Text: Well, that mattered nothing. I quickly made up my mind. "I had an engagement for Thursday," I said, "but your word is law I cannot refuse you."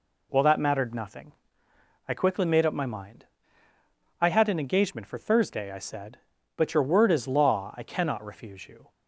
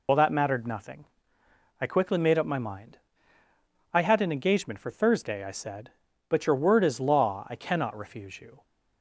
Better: first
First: none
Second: loses the start of "Well"; at 0.0 s; 60 ms

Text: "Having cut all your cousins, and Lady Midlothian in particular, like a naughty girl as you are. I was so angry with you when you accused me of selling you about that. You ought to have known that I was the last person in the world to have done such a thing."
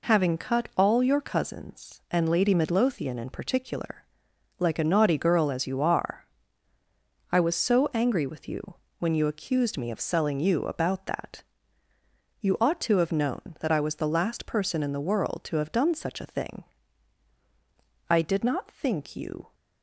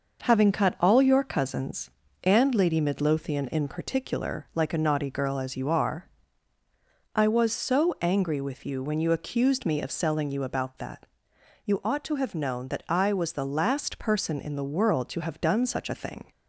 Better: second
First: pauses between "you" and "when"; slight; at 8.7 s; 0.24 s long // goes on to say "I did not think you"; from 18.1 s on; 1.4 s long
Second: none

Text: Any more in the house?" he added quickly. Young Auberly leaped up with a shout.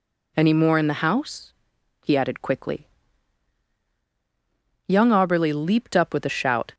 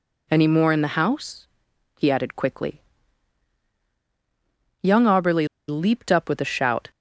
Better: first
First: none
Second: pauses between "Auberly" and "leaped"; slight; at 5.4 s; 0.20 s long

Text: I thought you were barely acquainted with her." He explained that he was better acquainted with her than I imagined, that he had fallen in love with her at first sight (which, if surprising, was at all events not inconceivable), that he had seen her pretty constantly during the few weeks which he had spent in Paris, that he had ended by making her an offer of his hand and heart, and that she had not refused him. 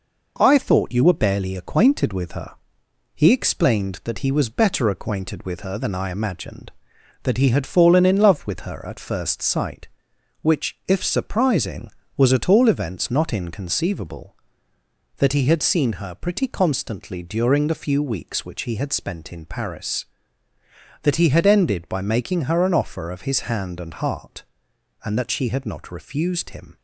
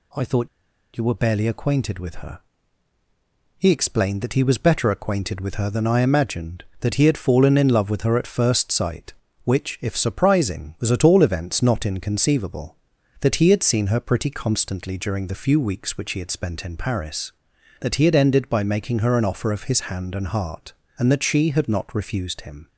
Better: first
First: none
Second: pauses between "thought" and "you"; noticeable; at 0.4 s; 0.47 s long

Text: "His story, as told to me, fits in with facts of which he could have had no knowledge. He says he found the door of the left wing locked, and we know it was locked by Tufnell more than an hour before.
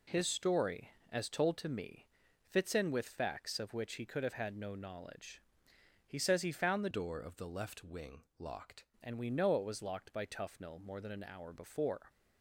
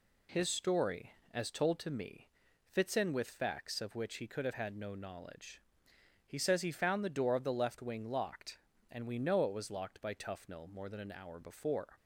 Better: second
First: changes voice from "door" to "locked"; from 6.9 to 8.8 s; 1.9 s long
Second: none

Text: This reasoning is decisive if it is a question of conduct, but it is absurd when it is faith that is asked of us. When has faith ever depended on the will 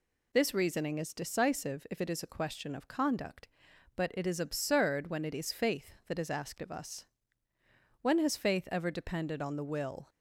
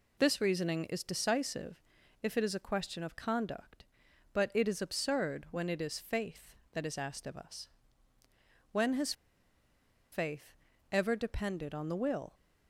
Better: first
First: none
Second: pauses between "decisive" and "if"; at 1.8 s; 0.42 s long // pauses between "has" and "faith"; at 9.1 s; 0.98 s long // pauses between "faith" and "ever"; slight; at 10.5 s; 0.36 s long

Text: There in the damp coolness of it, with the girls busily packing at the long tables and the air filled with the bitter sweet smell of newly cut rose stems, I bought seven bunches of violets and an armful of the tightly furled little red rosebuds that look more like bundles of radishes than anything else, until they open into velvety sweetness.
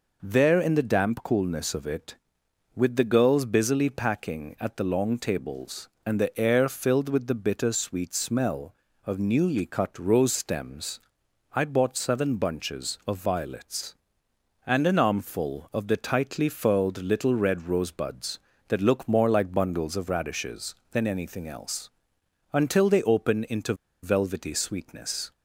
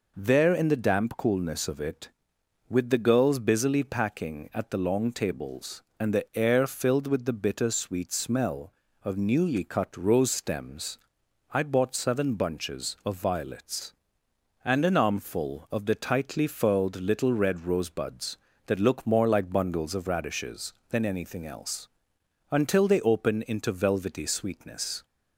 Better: second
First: pauses between "into" and "velvety"; slight; at 23.7 s; 0.28 s long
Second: none

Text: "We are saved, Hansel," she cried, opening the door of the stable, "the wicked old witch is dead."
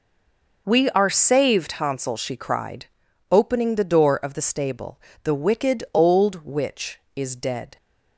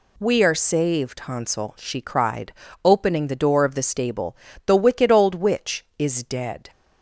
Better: second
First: stays silent before the first word; slight; until 0.6 s; 0.6 s long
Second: none

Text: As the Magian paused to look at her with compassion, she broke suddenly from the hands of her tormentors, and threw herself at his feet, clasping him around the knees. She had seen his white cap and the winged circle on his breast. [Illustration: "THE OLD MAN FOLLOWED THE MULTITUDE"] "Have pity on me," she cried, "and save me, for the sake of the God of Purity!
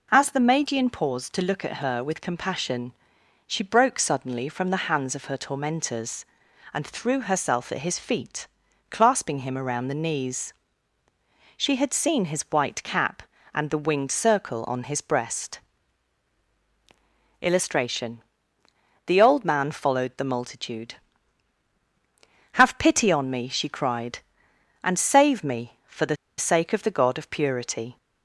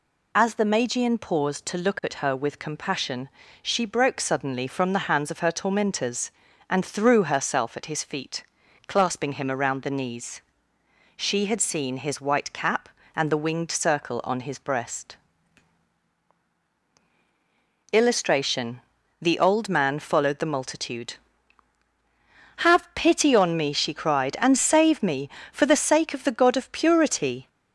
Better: second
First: pauses between "the" and "sake"; slight; at 26.1 s; 0.23 s long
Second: none

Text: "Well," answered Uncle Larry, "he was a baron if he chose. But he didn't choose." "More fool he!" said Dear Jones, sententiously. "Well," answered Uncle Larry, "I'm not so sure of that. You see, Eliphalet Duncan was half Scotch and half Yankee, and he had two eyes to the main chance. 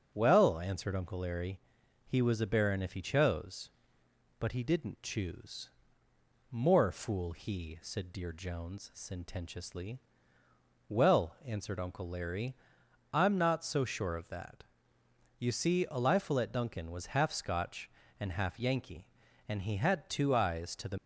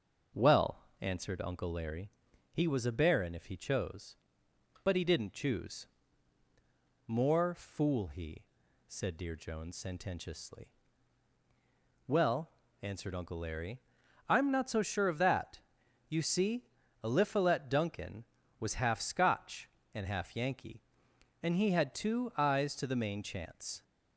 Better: second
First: starts louder than the rest; until 1.1 s; 6.5 dB // stops before "main chance"; at 20.9 s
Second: starts louder than the rest; noticeable; until 1.5 s; 6 dB

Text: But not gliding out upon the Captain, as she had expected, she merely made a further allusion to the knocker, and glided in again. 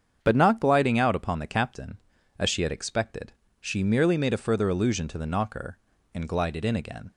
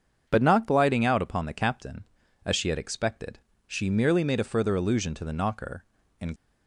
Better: first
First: starts louder than the rest; strong; until 1.2 s; 7.5 dB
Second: starts louder than the rest; until 1.2 s; 7 dB // stops before "glided in again"; at 6.3 s

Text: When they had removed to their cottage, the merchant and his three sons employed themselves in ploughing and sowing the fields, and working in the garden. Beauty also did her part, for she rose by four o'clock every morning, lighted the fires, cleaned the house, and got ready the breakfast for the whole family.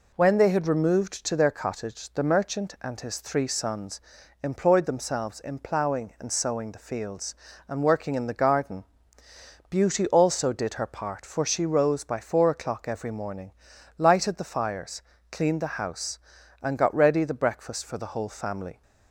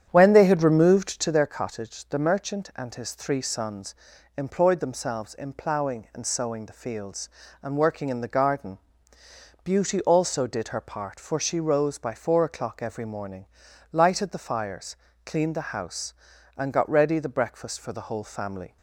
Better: first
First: pauses between "sons" and "employed"; at 3.9 s; 0.44 s long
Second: starts louder than the rest; strong; until 1.4 s; 9 dB // pauses between "sons" and "employed"; at 3.9 s; 0.44 s long

